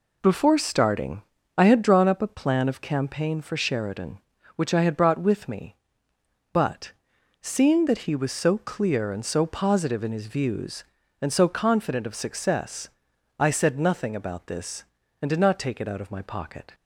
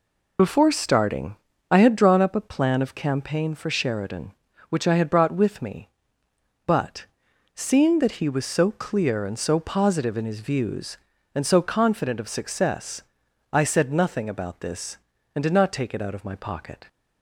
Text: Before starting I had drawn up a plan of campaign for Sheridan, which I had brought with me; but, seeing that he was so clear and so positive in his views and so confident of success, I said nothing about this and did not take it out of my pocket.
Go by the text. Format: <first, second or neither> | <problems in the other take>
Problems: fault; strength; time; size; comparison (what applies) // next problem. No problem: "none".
first | loses the start of "Before"; at 0.3 s; 35 ms // pauses between "starting" and "I"; slight; at 1.3 s; 0.34 s long; slight in the first